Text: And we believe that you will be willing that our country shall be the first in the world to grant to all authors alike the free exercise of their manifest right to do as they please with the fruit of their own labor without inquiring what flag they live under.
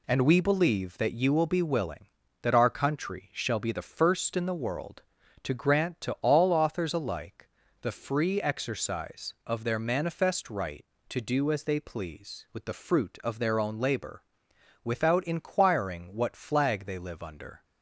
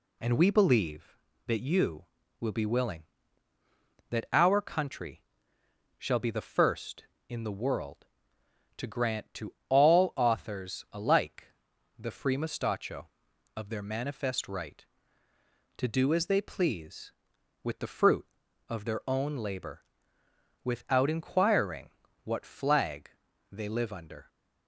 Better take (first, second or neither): first